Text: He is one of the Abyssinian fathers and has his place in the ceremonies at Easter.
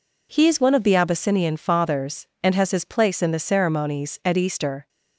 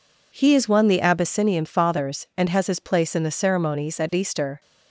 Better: first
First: none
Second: skips "of"; at 0.8 s

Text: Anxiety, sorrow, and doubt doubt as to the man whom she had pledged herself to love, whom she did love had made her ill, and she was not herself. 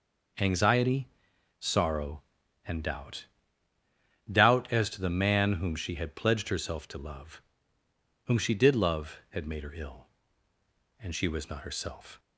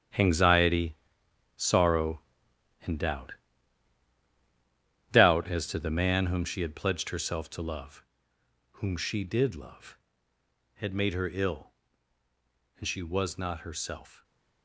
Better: first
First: starts louder than the rest; until 1.9 s; 6.5 dB // pauses between "doubt" and "doubt"; at 3.2 s; 1.0 s long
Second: gets quieter; strong; throughout; 12 dB // starts louder than the rest; strong; until 1.7 s; 9.5 dB // pauses between "doubt" and "doubt"; strong; at 3.3 s; 1.8 s long

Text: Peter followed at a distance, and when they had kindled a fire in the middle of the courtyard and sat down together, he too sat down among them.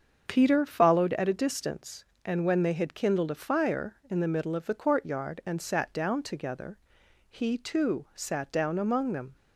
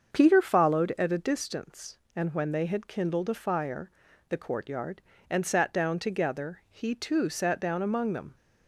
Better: first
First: starts louder than the rest; until 1.2 s; 7 dB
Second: starts louder than the rest; until 1.1 s; 7 dB // skips "in the middle of"; at 4.0 s

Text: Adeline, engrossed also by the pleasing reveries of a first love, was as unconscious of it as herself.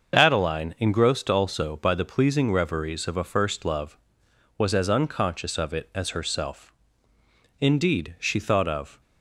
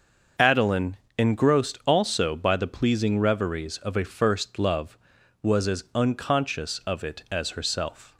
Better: second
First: starts louder than the rest; until 1.1 s; 6.5 dB // goes on to say "Indeed she thought of"; from 7.6 s on; 1.4 s long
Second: starts louder than the rest; until 1.5 s; 6.5 dB

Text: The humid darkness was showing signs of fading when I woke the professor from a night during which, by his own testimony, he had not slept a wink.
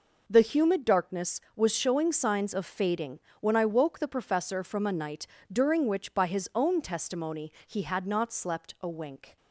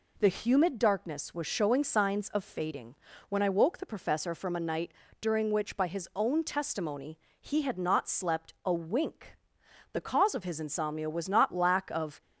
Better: first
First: pauses between "fading" and "when"; slight; at 3.2 s; 0.20 s long // pauses between "night" and "during"; slight; at 5.2 s; 0.24 s long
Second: pauses between "fading" and "when"; slight; at 2.9 s; 0.34 s long // pauses between "night" and "during"; slight; at 4.9 s; 0.30 s long // goes on to say "The cause of his insomnia was not lack of"; strong; from 9.9 s on; 2.2 s long

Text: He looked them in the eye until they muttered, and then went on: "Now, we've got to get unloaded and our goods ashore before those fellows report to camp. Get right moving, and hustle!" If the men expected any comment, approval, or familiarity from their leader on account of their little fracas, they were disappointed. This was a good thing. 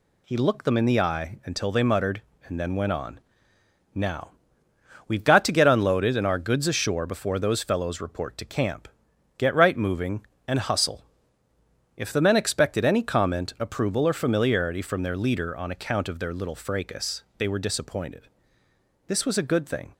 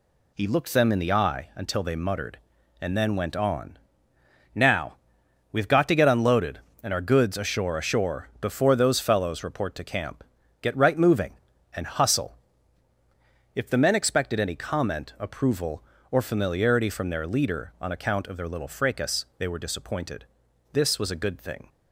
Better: first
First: none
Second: says "ashore" twice; at 7.7 s

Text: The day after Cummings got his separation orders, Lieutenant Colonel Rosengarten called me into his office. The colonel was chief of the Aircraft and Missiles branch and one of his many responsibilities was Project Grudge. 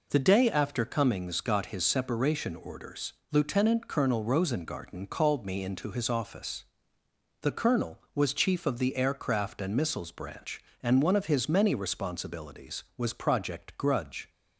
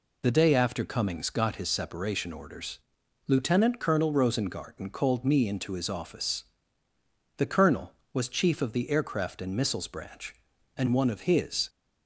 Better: first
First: none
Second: stops before "many responsibilities was Project Grudge"; at 11.6 s

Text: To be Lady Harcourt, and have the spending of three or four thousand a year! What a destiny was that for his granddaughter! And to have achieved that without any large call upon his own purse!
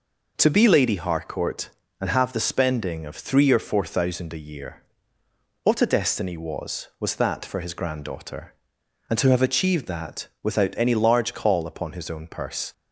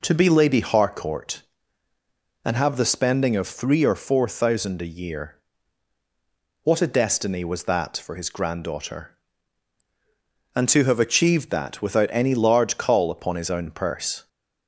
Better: second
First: says "was" twice; at 6.9 s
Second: none

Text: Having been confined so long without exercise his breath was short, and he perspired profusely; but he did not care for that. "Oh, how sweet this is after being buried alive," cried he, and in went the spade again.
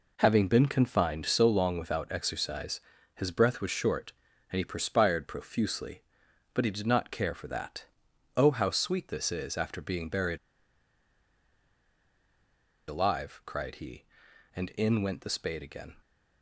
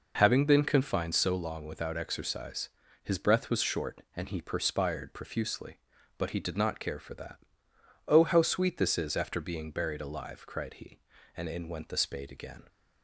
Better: second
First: pauses between "exercise" and "his"; slight; at 2.7 s; 0.36 s long // pauses between "buried" and "alive"; strong; at 10.3 s; 2.5 s long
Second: pauses between "exercise" and "his"; slight; at 2.6 s; 0.34 s long

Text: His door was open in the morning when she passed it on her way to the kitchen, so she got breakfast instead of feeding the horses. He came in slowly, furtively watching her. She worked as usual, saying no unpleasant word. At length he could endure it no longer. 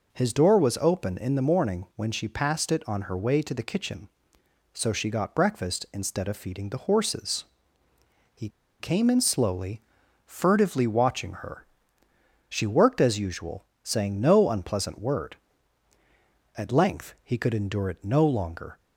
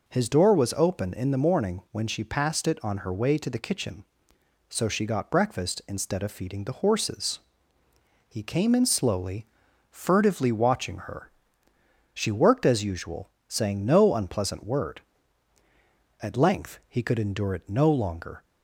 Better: second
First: pauses between "He" and "came"; slight; at 8.4 s; 0.31 s long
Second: none

